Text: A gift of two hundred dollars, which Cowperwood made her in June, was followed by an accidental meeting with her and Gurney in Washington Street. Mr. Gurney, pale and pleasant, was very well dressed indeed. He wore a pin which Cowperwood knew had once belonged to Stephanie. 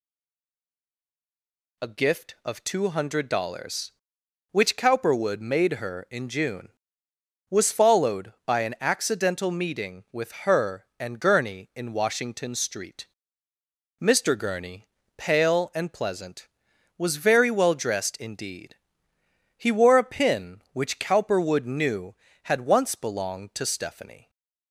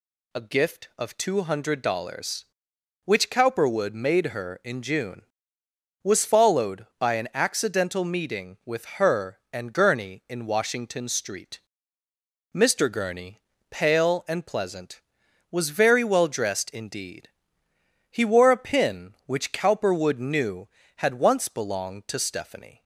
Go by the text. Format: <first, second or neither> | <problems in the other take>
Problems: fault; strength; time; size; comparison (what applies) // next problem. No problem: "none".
second | stays silent before the first word; noticeable; until 1.7 s; 1.7 s long